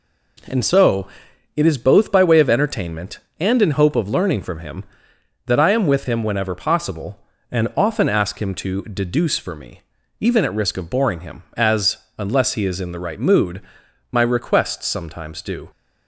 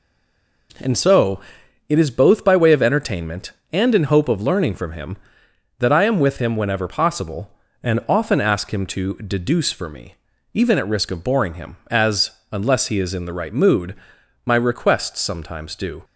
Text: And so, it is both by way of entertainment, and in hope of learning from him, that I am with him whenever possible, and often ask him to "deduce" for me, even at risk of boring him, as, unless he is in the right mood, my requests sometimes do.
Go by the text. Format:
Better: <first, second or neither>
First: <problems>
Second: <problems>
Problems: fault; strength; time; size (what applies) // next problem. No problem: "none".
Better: first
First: none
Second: stays silent before the first word; slight; until 0.6 s; 0.6 s long